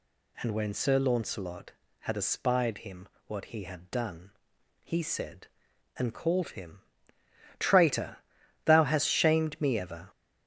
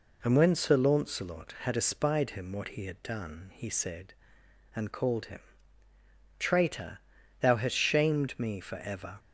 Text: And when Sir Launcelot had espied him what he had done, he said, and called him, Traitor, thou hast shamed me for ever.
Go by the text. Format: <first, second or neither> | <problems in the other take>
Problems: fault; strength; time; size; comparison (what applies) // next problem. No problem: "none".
second | pauses between "him" and "what"; slight; at 3.0 s; 0.20 s long // skips "for"; at 9.7 s